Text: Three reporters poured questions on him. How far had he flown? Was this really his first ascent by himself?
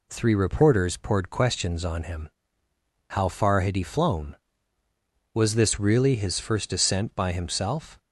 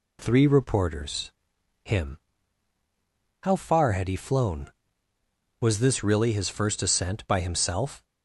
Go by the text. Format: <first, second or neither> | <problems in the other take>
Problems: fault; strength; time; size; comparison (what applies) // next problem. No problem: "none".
first | skips "poured questions on"; at 1.5 s